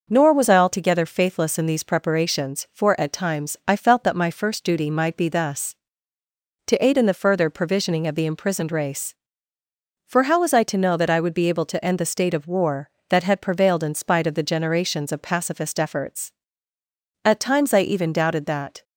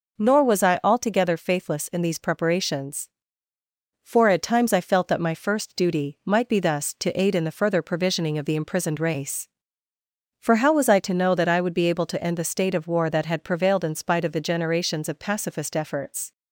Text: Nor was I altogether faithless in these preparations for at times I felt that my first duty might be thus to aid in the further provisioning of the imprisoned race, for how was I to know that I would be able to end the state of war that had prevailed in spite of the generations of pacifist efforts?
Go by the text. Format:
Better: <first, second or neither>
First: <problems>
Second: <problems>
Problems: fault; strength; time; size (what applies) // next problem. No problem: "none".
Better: second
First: goes on to say "At times I even doubted that"; from 17.2 s on; 1.6 s long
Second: none